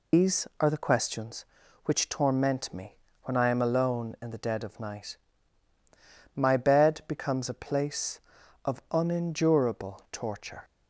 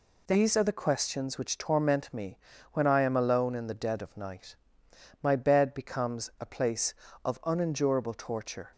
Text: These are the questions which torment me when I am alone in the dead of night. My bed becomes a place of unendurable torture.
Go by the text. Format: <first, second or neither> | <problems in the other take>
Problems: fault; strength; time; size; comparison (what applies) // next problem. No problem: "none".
second | loses the start of "These"; at 0.1 s; 155 ms // pauses between "me" and "when"; slight; at 2.9 s; 0.28 s long; slight in the second